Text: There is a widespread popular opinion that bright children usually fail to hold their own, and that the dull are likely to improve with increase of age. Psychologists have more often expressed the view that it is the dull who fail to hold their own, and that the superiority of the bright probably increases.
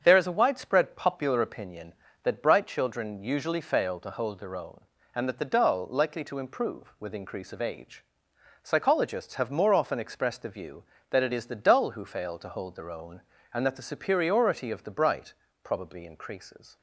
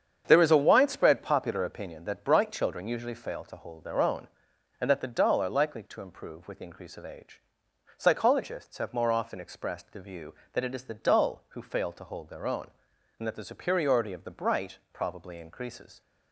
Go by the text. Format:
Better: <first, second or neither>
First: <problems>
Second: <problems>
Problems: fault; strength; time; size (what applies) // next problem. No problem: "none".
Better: second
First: starts louder than the rest; strong; until 1.0 s; 7 dB // skips "are"; at 5.8 s // pauses between "bright" and "probably"; slight; at 15.3 s; 0.30 s long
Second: starts louder than the rest; strong; until 1.2 s; 8 dB // pauses between "bright" and "probably"; slight; at 14.7 s; 0.16 s long